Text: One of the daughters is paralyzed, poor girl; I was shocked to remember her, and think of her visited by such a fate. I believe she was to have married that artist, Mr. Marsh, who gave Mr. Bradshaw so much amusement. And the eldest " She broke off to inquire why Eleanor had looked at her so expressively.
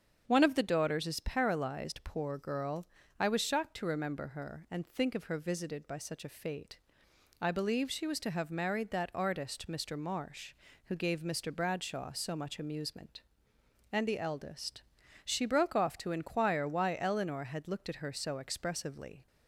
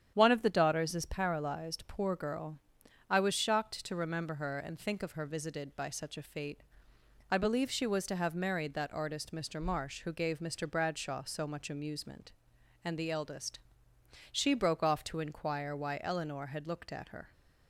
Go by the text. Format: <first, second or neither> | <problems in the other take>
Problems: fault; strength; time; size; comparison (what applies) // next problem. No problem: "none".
first | starts louder than the rest; strong; until 1.1 s; 9 dB; strong in the first // stops before "so expressively"; at 17.3 s